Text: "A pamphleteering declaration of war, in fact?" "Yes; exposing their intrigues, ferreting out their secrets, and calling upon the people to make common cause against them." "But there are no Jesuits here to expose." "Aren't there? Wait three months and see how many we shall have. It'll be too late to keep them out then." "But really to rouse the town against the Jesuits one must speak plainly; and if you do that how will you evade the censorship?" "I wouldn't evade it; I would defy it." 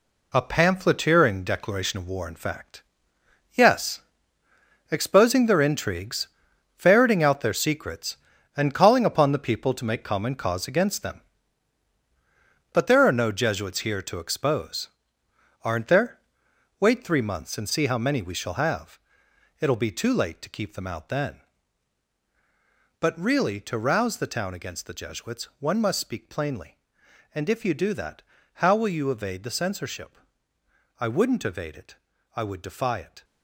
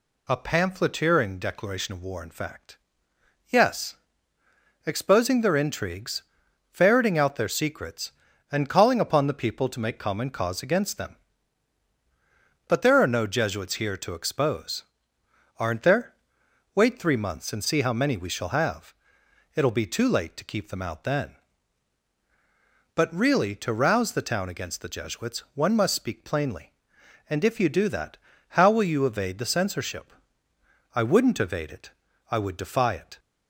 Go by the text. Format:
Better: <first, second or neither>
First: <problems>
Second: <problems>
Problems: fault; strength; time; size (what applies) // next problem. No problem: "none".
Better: second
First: gets quieter; strong; throughout; 8 dB // pauses between "that" and "how"; at 28.2 s; 0.38 s long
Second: pauses between "that" and "how"; at 28.1 s; 0.38 s long